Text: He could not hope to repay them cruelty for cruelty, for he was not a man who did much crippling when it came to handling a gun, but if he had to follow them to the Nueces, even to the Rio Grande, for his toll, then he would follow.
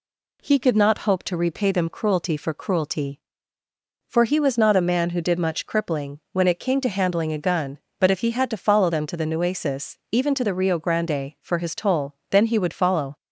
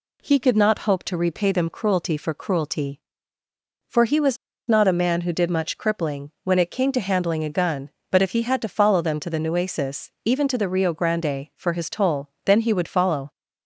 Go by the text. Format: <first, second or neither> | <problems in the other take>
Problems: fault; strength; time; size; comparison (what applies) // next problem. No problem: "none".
first | pauses between "was" and "not"; slight; at 4.3 s; 0.32 s long